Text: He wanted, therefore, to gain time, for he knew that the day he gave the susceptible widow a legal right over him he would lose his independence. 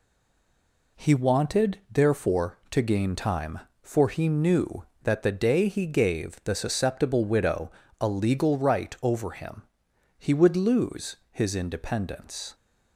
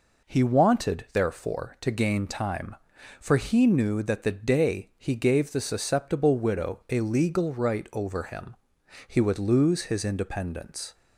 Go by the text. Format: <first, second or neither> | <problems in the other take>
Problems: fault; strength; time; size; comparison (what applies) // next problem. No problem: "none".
second | stays silent before the first word; until 0.9 s; 0.9 s long // pauses between "widow" and "a"; slight; at 7.6 s; 0.30 s long // pauses between "him" and "he"; noticeable; at 9.6 s; 0.56 s long; noticeable in the second